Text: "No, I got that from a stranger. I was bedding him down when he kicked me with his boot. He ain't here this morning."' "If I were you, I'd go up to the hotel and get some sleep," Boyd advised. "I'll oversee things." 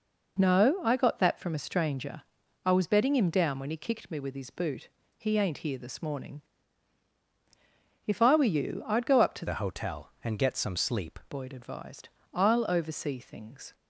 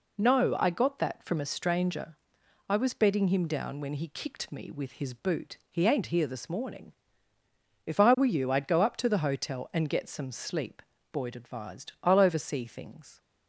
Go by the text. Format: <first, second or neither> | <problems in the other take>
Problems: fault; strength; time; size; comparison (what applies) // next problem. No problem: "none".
second | changes voice from "the" to "sleep"; from 9.4 to 11.1 s; 1.7 s long